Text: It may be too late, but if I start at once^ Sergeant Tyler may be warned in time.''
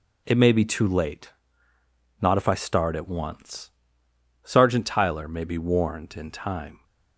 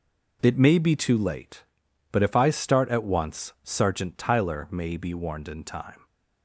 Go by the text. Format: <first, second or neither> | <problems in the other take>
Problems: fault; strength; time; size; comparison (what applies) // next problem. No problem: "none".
second | says "not" for "but"; at 2.2 s // pauses between "once" and "Sergeant"; noticeable; at 3.7 s; 0.74 s long